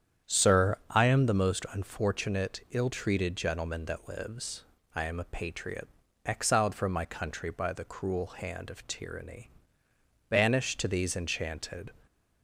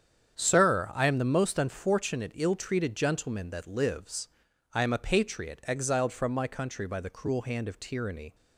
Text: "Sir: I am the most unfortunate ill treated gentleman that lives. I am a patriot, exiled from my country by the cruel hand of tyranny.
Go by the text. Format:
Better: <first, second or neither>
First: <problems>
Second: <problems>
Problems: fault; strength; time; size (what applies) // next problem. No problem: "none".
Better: second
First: starts louder than the rest; strong; until 1.4 s; 9 dB // goes on to say "Banished to these Enchanted"; from 10.2 s on; 1.6 s long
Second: starts louder than the rest; strong; until 1.3 s; 8 dB